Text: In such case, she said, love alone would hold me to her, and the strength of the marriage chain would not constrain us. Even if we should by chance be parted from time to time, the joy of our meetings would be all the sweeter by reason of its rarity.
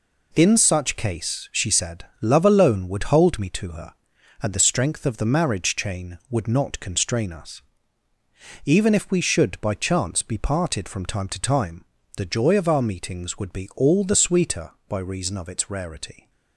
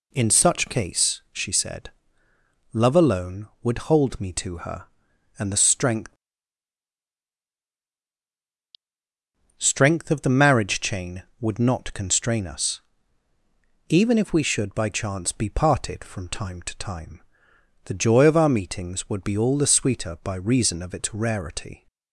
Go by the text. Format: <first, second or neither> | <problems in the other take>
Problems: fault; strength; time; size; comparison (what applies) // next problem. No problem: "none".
first | says "strength" twice; at 9.5 s